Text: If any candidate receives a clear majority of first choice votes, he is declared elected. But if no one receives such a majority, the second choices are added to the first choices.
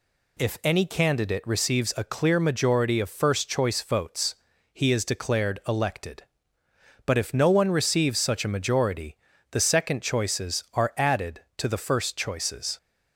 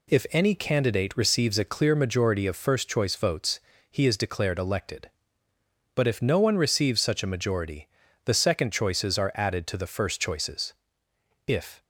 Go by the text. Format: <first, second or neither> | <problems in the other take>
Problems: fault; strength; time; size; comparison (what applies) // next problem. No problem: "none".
first | goes on to say "If"; slight; from 11.4 s on; 0.38 s long